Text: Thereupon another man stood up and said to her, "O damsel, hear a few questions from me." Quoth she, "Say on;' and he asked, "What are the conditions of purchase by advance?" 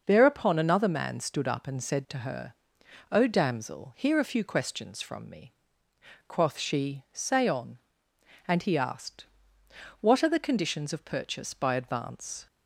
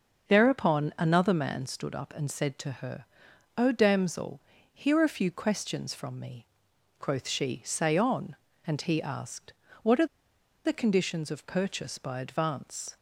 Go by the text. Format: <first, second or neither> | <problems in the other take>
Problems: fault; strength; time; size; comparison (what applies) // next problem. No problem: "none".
first | starts louder than the rest; until 1.3 s; 6 dB; noticeable in the first // pauses between "are" and "the"; noticeable; at 10.0 s; 0.58 s long